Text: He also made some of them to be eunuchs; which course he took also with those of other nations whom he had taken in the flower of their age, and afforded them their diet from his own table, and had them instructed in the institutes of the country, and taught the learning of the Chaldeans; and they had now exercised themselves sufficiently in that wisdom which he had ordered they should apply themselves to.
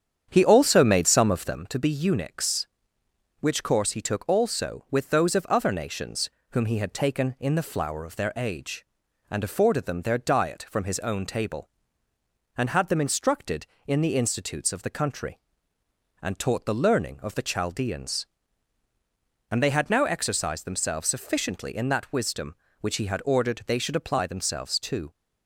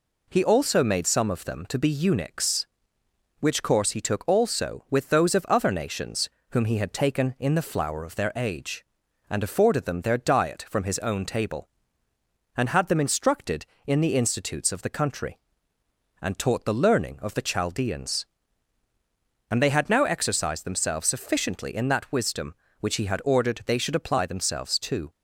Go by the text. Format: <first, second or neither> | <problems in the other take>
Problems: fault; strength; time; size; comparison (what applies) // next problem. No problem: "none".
second | starts louder than the rest; strong; until 1.6 s; 8.5 dB // pauses between "nations" and "whom"; slight; at 6.2 s; 0.22 s long; slight in the second